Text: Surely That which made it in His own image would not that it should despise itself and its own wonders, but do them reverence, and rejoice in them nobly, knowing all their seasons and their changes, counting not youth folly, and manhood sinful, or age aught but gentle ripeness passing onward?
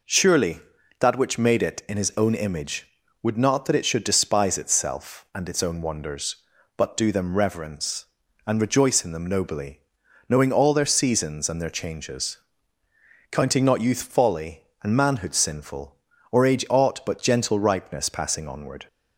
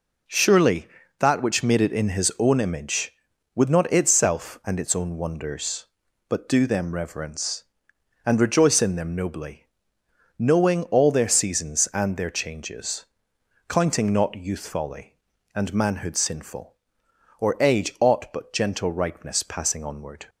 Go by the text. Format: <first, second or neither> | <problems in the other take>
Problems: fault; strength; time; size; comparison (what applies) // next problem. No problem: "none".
first | skips "that it should despise"; at 3.9 s